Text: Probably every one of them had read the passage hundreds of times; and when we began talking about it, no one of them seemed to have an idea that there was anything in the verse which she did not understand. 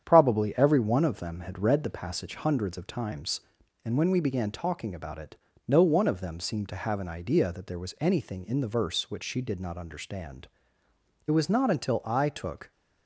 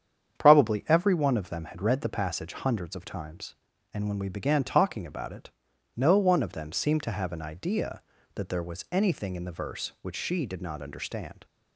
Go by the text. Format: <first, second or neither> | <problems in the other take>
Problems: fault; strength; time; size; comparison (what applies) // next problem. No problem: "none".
second | starts louder than the rest; strong; until 1.0 s; 8.5 dB; strong in the second // goes on to say "It was not until I took"; from 11.2 s on; 1.4 s long